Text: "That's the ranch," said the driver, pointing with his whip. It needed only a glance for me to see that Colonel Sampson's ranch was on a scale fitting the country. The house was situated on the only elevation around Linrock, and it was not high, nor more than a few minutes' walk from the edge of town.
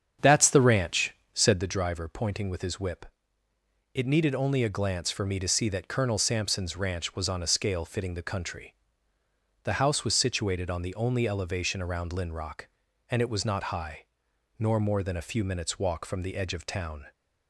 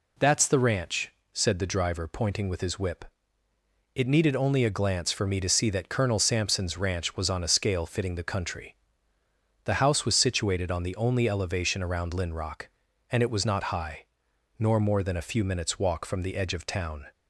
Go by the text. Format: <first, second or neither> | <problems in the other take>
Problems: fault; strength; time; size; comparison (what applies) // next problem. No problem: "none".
second | starts louder than the rest; strong; until 1.7 s; 8 dB